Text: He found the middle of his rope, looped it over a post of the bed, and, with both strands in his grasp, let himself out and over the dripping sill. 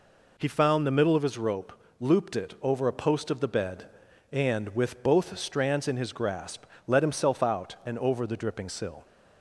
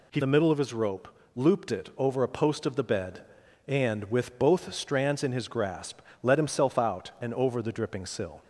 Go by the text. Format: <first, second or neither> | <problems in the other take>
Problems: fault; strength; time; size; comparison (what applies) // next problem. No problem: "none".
first | skips "found"; at 0.2 s